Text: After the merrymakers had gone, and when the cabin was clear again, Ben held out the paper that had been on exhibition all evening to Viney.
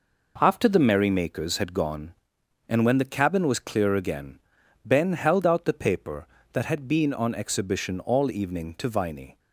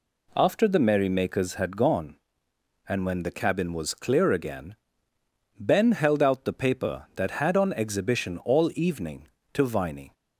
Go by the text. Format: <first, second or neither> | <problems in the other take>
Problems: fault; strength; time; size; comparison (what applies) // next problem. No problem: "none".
first | skips "been"; at 7.5 s